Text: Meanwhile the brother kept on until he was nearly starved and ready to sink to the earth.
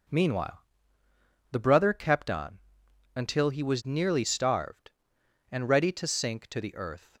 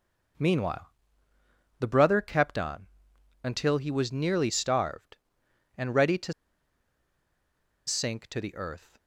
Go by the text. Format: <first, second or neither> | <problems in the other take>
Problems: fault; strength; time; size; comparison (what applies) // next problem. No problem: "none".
first | pauses between "Meanwhile" and "the"; noticeable; at 0.9 s; 0.88 s long; noticeable in the first // pauses between "on" and "until"; noticeable; at 2.8 s; 0.56 s long; noticeable in the first // pauses between "to" and "sink"; strong; at 6.3 s; 1.5 s long